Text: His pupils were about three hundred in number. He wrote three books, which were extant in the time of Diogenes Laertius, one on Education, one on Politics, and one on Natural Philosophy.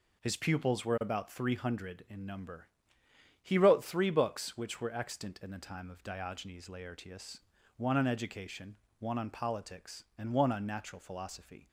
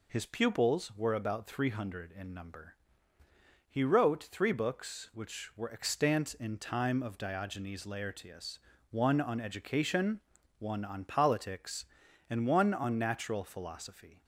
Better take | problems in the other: first | skips "the"; at 6.5 s

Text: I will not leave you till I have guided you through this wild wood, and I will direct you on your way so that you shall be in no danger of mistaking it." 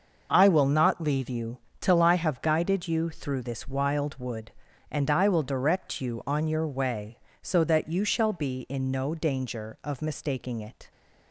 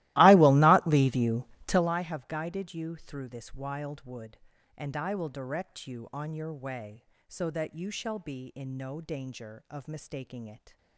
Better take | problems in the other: first | starts louder than the rest; strong; until 1.9 s; 18 dB // pauses between "you" and "till"; slight; at 1.4 s; 0.24 s long; slight in the first

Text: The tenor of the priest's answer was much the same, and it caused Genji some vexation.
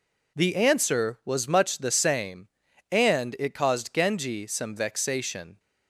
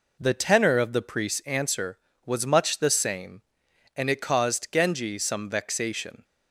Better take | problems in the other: second | skips "tenor of the priest's"; at 0.5 s

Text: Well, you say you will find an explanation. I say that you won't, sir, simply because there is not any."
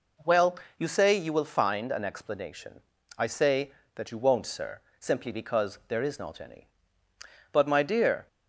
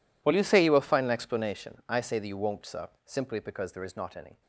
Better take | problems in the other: second | goes on to say "But my dear"; noticeable; from 7.5 s on; 0.76 s long

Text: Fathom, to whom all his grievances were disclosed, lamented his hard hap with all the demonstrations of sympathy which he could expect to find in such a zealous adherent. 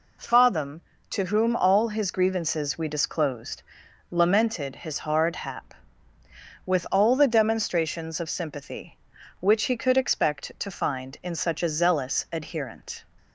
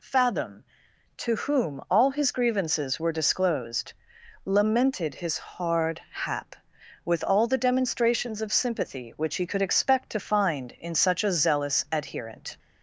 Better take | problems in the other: second | says "we" for "were"; at 2.7 s

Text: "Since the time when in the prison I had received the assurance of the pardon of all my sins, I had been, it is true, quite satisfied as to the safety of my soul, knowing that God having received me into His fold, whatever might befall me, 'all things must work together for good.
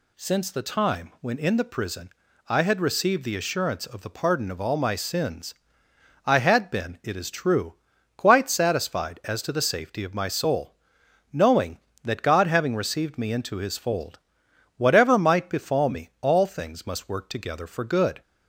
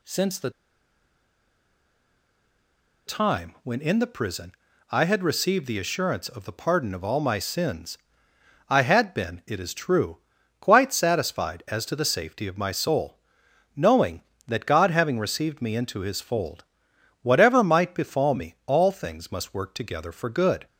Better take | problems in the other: first | pauses between "the" and "time"; strong; at 0.4 s; 2.5 s long // pauses between "prison" and "I"; slight; at 4.5 s; 0.36 s long; slight in the first

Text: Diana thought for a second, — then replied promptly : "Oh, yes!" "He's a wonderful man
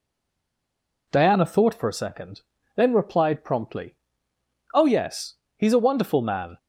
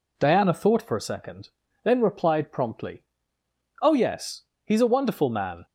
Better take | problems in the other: second | stays silent before the first word; until 1.0 s; 1.0 s long

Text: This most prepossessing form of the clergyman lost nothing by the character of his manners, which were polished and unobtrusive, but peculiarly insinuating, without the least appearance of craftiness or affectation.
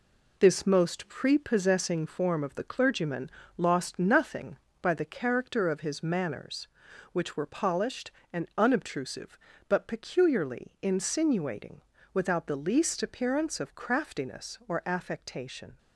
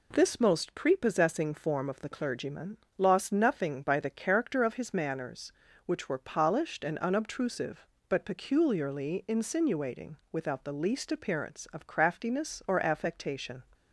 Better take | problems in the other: second | gets quieter; noticeable; throughout; 5.5 dB // pauses between "clergyman" and "lost"; slight; at 3.2 s; 0.26 s long; slight in the second

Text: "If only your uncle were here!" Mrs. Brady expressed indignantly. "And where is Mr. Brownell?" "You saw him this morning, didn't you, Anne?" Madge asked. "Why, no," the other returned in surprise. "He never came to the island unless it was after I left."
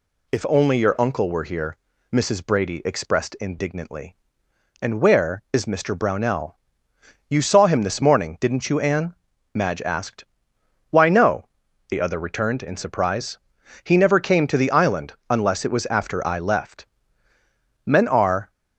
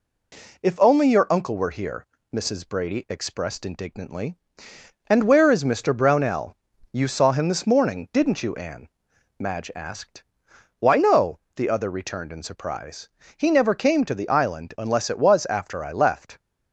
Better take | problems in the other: second | pauses between "island" and "unless"; slight; at 15.1 s; 0.16 s long // goes on to say "Men are"; noticeable; from 17.8 s on; 0.64 s long

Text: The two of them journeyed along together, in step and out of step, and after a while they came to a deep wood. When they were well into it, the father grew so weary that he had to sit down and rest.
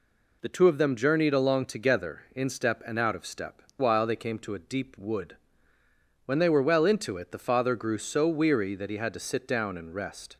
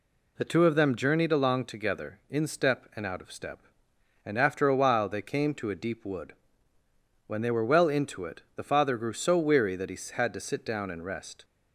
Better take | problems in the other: second | skips "and after a"; at 3.7 s

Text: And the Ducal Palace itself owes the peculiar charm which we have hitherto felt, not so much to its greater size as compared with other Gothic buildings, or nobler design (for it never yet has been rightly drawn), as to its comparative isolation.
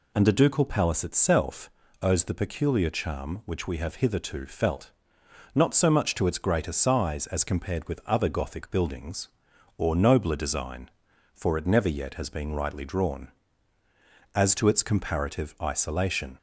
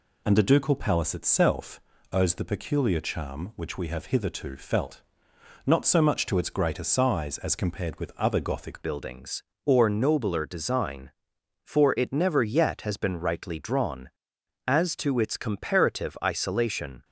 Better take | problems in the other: first | pauses between "itself" and "owes"; slight; at 1.8 s; 0.32 s long; slight in the first // changes voice at "buildings"; from 8.8 s on; 8.2 s long

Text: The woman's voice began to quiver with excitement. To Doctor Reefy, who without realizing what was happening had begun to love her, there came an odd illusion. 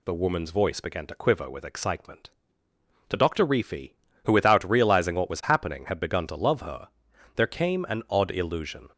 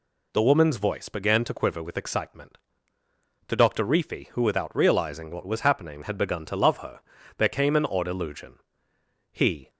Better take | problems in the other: first | goes on to say "He"; slight; from 9.3 s on; 0.38 s long

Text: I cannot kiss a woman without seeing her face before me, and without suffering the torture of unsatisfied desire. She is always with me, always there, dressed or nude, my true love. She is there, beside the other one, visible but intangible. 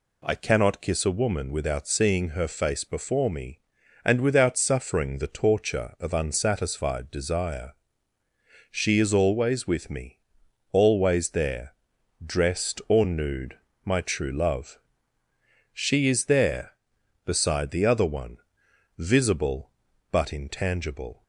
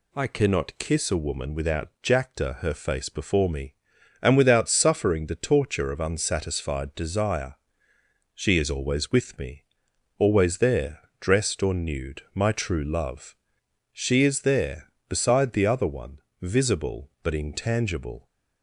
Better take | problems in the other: first | says "jacta" for "seeing"; at 2.0 s

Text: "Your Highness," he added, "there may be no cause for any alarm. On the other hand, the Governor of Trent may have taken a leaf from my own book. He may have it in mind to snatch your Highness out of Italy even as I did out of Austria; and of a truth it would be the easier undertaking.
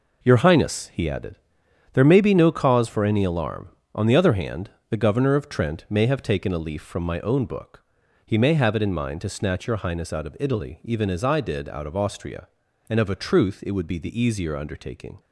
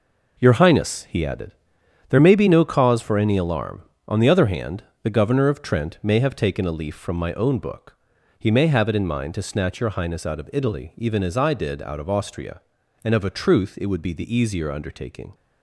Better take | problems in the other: neither | none

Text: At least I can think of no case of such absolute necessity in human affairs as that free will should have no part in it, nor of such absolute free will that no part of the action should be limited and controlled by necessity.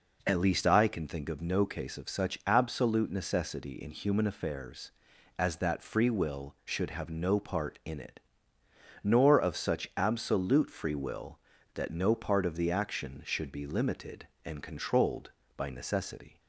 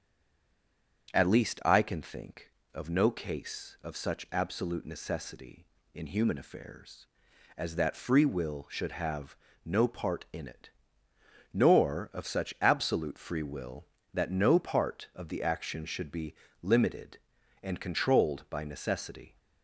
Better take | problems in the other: first | stays silent before the first word; until 1.0 s; 1.0 s long // starts louder than the rest; strong; until 2.1 s; 8 dB // pauses between "have" and "no"; slight; at 9.3 s; 0.30 s long // pauses between "be" and "limited"; slight; at 16.3 s; 0.28 s long

